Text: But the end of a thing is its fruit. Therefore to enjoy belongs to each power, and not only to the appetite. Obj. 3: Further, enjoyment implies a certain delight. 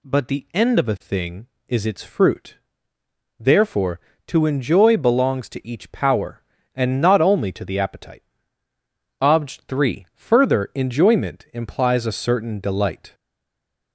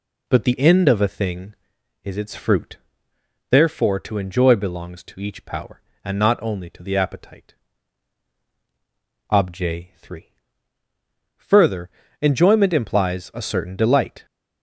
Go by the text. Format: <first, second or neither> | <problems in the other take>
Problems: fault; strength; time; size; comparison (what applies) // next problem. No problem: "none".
second | stays silent after the last word; slight; from 13.1 s on; 0.8 s long